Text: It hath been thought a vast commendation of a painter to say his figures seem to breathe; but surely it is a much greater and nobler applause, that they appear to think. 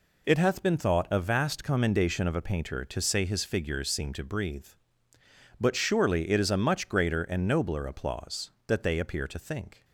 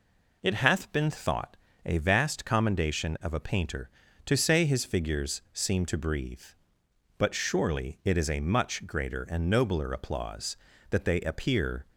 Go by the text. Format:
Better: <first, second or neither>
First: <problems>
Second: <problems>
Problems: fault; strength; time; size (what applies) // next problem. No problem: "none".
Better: first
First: none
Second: pauses between "thought" and "a"; slight; at 1.5 s; 0.28 s long // stops before "to think"; at 11.9 s